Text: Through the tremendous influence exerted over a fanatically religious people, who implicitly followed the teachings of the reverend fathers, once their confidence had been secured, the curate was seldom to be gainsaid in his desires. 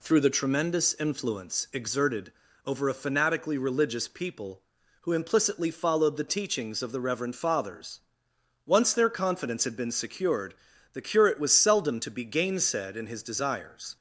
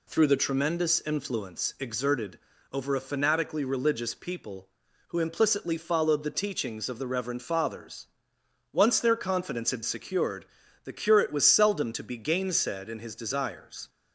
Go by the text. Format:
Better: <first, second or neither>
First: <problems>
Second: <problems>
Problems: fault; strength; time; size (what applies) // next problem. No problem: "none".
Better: first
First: pauses between "exerted" and "over"; slight; at 2.3 s; 0.34 s long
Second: pauses between "exerted" and "over"; slight; at 2.3 s; 0.34 s long // skips "been"; at 9.8 s